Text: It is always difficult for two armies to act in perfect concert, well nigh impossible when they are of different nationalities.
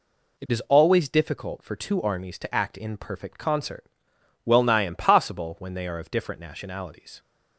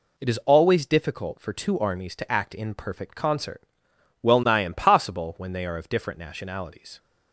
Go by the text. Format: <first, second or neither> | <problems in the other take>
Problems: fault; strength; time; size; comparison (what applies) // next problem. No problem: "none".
neither | none